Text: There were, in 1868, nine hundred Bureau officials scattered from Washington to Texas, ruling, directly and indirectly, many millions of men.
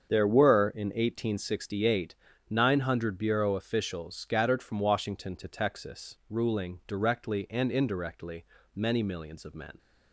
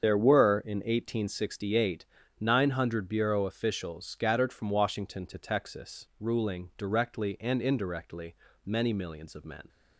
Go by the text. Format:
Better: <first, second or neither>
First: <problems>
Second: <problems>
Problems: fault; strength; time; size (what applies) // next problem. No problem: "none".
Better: first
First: starts louder than the rest; strong; until 1.1 s; 7 dB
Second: loses the start of "There"; at 0.0 s; 35 ms // starts louder than the rest; strong; until 1.1 s; 7 dB